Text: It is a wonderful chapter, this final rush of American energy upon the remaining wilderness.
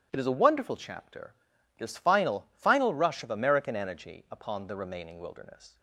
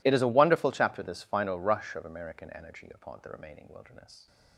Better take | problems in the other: second | starts louder than the rest; strong; until 1.1 s; 11.5 dB // says "final" twice; at 2.5 s

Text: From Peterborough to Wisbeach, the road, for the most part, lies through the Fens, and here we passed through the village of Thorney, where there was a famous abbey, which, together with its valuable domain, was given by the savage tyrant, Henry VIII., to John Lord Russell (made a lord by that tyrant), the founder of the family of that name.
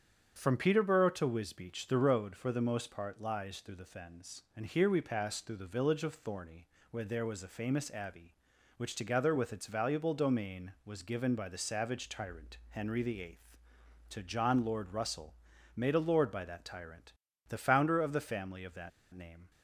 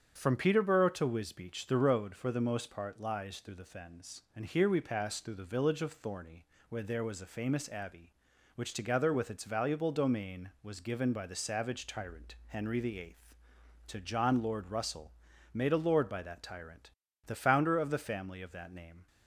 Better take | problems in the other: second | starts louder than the rest; strong; until 1.3 s; 8 dB; strong in the second // pauses between "that" and "name"; slight; at 18.9 s; 0.23 s long

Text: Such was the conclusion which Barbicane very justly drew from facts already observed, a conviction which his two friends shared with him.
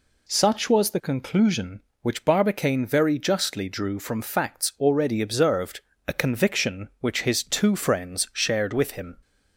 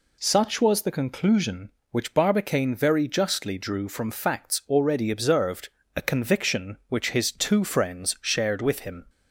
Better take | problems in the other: neither | none

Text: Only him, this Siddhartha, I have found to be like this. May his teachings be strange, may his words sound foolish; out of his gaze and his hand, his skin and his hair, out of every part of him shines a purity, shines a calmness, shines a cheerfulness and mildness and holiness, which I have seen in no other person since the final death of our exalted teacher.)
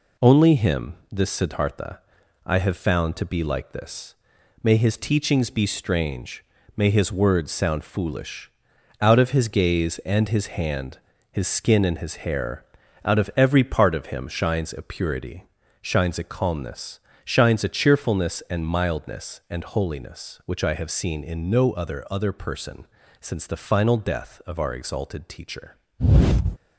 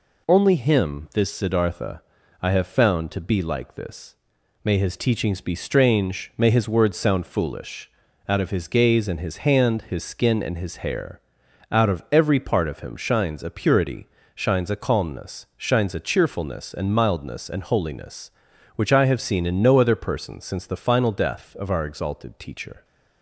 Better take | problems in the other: second | says "other" twice; at 22.0 s // pauses between "person" and "since"; slight; at 22.8 s; 0.32 s long

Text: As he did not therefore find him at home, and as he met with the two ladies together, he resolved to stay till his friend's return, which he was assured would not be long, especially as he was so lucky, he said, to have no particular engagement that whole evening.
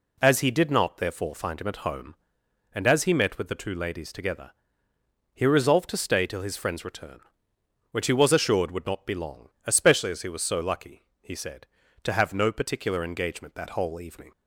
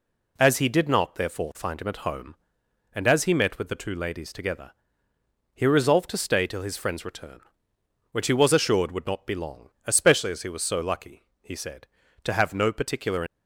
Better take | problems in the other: first | stops before "engagement that whole evening"; at 13.2 s

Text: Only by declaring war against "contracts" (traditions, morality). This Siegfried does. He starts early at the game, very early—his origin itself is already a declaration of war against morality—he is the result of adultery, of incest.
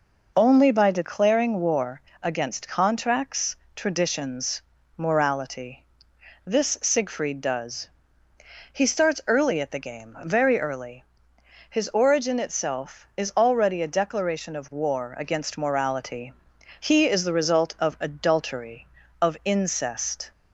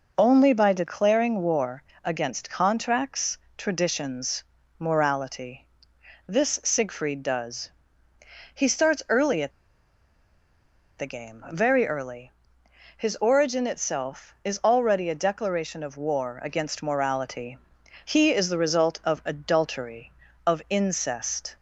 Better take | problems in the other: first | pauses between "war" and "against"; slight; at 1.8 s; 0.22 s long; slight in the first // pauses between "at" and "the"; strong; at 9.5 s; 1.4 s long

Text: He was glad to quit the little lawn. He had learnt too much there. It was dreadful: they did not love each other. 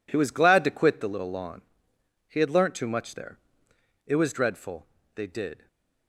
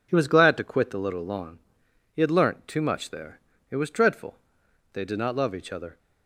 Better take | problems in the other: second | stops before "not love each other"; at 5.6 s

